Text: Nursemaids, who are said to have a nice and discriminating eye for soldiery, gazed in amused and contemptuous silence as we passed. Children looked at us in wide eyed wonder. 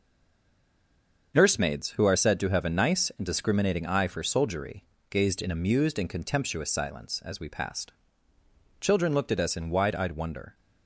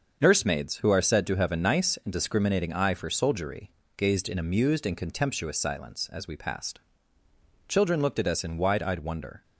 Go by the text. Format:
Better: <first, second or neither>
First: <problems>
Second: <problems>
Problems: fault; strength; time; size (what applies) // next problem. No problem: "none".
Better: second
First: stays silent before the first word; noticeable; until 1.3 s; 1.3 s long // starts louder than the rest; until 2.3 s; 6.5 dB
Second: starts louder than the rest; until 1.2 s; 6.5 dB